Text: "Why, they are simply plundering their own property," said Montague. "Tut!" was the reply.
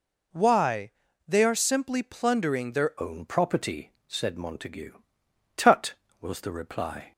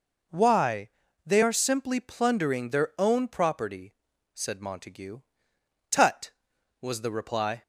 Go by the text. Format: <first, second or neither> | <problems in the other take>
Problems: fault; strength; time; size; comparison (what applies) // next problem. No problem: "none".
second | changes voice at "own"; from 3.0 s on; 4.1 s long